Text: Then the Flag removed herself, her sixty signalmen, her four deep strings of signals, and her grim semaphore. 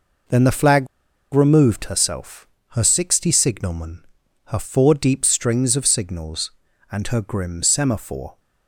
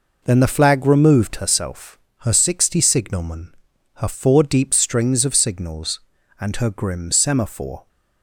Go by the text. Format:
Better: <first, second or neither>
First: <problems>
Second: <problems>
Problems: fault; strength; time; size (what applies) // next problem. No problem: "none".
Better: second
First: pauses between "Flag" and "removed"; noticeable; at 0.8 s; 0.46 s long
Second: none